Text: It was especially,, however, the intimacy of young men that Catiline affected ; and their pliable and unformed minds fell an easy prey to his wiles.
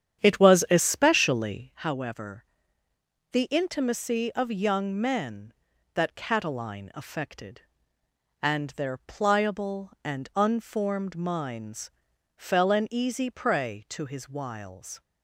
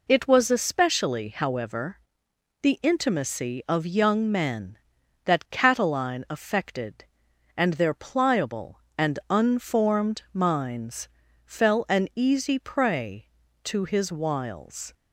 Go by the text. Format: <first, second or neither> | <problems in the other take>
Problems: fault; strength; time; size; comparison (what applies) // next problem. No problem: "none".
second | starts louder than the rest; strong; until 1.7 s; 9 dB // pauses between "minds" and "fell"; at 11.9 s; 0.44 s long; slight in the second